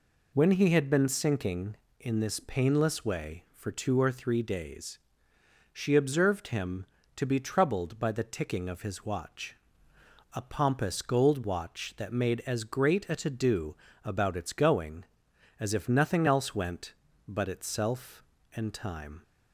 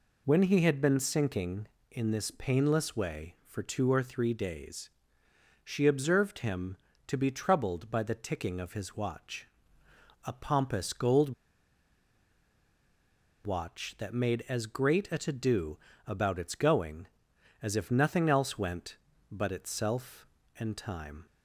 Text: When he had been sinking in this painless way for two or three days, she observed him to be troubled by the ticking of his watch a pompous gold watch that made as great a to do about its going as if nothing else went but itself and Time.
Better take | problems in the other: first | pauses between "watch" and "a"; noticeable; at 9.4 s; 0.78 s long; noticeable in the first // pauses between "gold" and "watch"; strong; at 11.3 s; 2.1 s long // pauses between "do" and "about"; slight; at 15.7 s; 0.30 s long; slight in the first

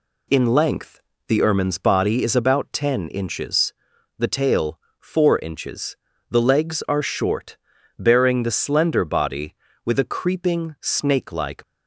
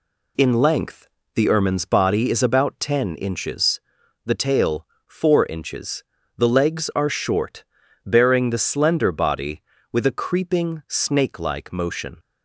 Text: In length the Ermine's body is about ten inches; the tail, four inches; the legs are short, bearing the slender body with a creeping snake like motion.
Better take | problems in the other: second | pauses between "length" and "the"; slight; at 1.0 s; 0.26 s long; slight in the second // stops before "motion"; at 11.6 s

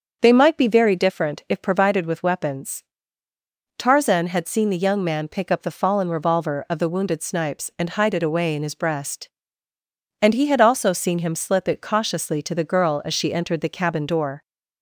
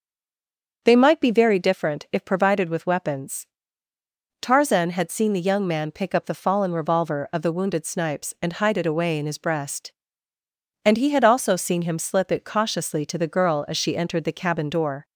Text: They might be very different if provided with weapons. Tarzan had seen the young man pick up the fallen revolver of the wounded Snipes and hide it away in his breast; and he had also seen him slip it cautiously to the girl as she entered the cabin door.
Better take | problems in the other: first | stays silent before the first word; slight; until 0.8 s; 0.8 s long // starts louder than the rest; until 1.8 s; 7 dB; also in the first

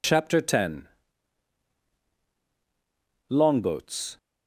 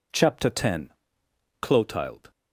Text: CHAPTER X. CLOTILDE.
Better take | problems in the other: second | says "Longboats" for "CLOTILDE"; at 3.3 s

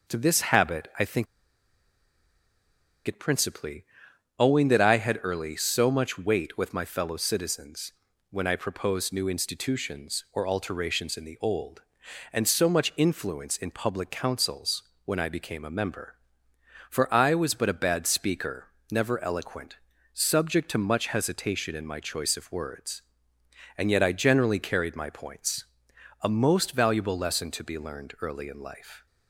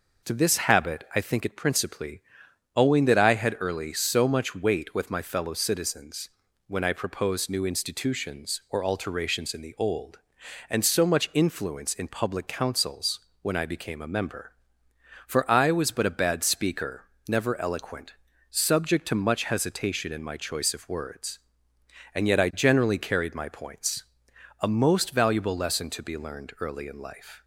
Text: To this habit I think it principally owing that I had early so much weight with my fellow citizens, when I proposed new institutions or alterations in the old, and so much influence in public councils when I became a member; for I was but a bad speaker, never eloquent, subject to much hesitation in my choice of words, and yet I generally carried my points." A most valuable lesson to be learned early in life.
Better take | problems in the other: second | pauses between "think" and "it"; strong; at 1.2 s; 1.8 s long // pauses between "principally" and "owing"; noticeable; at 3.8 s; 0.54 s long; noticeable in the second // pauses between "councils" and "when"; slight; at 14.8 s; 0.24 s long; slight in the second

